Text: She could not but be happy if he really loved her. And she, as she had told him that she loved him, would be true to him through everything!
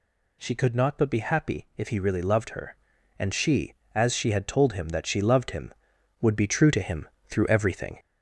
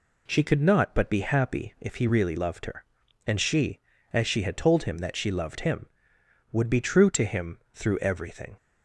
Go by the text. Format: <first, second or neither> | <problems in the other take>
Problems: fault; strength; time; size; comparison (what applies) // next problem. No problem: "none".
second | gets louder; slight; throughout; 3 dB // pauses between "him" and "through"; slight; at 7.0 s; 0.20 s long; slight in the second